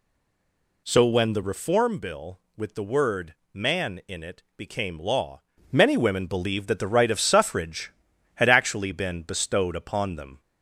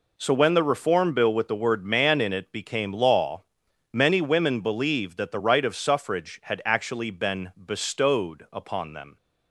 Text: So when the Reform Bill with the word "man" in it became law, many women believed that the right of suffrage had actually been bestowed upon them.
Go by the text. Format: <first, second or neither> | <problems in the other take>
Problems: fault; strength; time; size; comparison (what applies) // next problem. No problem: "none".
second | stays silent before the first word; slight; until 0.8 s; 0.8 s long // pauses between "word" and "man"; slight; at 3.3 s; 0.18 s long